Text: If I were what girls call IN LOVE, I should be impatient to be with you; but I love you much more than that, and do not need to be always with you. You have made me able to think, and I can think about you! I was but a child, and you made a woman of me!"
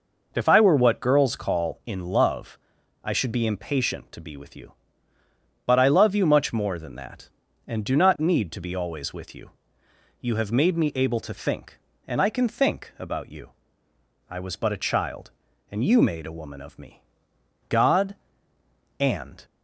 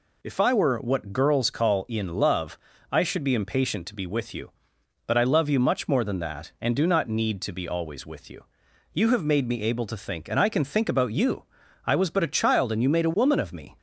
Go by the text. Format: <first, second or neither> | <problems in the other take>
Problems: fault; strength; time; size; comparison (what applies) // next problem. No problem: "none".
second | goes on to say "God and"; strong; from 17.6 s on; 1.7 s long